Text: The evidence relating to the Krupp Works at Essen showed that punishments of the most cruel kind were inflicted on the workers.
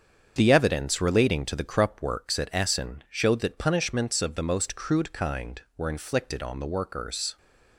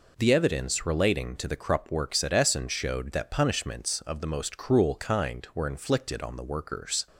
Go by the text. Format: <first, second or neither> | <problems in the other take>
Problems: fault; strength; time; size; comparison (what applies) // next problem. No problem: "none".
second | starts louder than the rest; strong; until 1.3 s; 7.5 dB // says "crude" for "cruel"; at 4.7 s